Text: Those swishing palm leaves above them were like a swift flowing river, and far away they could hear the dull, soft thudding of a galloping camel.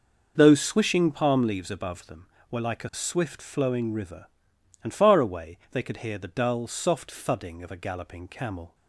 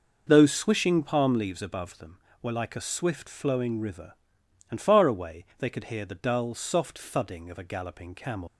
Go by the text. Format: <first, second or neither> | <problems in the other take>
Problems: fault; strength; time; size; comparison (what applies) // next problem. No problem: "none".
first | leaves "camel" unfinished; at 8.4 s; 125 ms